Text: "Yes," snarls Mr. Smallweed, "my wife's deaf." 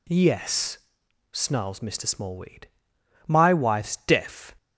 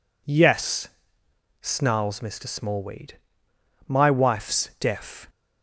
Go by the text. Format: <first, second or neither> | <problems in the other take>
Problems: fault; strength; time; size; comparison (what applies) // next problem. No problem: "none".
neither | none